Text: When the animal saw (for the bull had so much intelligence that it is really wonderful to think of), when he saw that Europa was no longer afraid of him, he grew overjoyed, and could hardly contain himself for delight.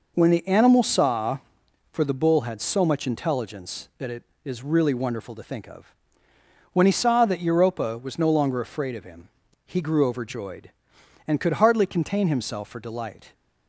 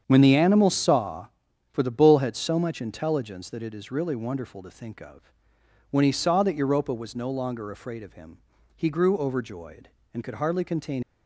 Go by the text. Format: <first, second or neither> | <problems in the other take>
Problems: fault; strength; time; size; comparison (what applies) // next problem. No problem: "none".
first | starts louder than the rest; strong; until 1.0 s; 8 dB // stops before "himself for delight"; at 11.0 s